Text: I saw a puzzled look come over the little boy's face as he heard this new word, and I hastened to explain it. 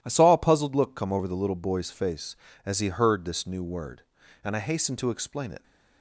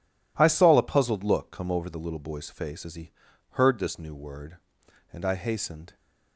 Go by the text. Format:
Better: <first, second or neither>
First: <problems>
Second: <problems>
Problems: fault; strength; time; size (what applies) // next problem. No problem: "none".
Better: first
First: none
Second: pauses between "he" and "heard"; at 3.0 s; 0.42 s long // stops before "to explain it"; at 5.9 s